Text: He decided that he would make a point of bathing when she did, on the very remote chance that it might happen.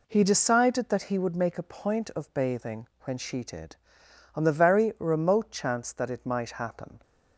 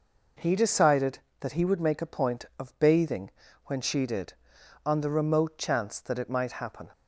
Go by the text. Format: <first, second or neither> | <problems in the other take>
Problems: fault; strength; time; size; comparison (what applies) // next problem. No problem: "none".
first | pauses between "bathing" and "when"; slight; at 3.3 s; 0.34 s long; slight in the first // skips "very"; at 5.0 s